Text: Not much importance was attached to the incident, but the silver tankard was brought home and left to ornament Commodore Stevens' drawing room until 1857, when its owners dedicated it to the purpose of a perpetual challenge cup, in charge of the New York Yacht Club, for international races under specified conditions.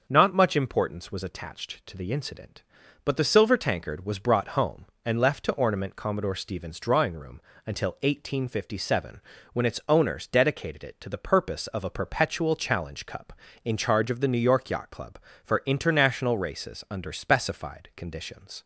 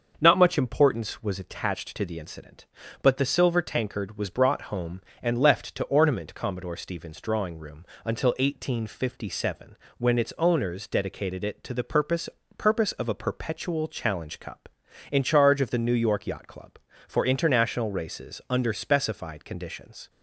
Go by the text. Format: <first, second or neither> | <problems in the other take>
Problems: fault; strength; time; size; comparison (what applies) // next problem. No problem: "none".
first | starts louder than the rest; until 1.2 s; 6 dB // pauses between "room" and "until"; slight; at 7.8 s; 0.20 s long; slight in the first // says "purpose" twice; at 12.5 s